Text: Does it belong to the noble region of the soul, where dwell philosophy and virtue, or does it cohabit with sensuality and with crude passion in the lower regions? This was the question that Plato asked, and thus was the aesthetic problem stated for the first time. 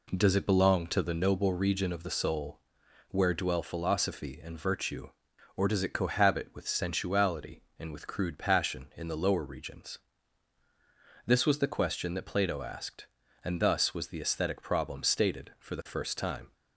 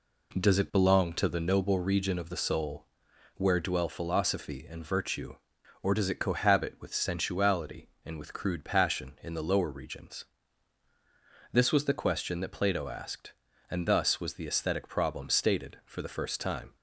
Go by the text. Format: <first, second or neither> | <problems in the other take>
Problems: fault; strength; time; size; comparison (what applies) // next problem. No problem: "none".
neither | none